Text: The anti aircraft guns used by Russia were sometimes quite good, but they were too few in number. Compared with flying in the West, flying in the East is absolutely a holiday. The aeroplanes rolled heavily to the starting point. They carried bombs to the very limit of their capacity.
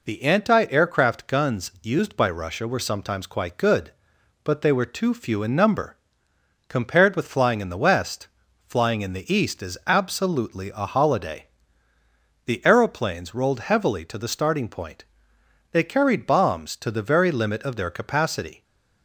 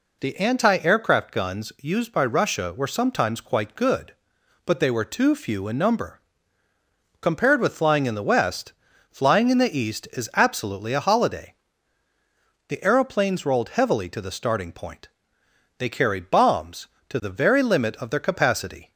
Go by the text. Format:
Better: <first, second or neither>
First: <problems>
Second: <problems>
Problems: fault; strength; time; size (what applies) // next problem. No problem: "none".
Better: neither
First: none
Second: none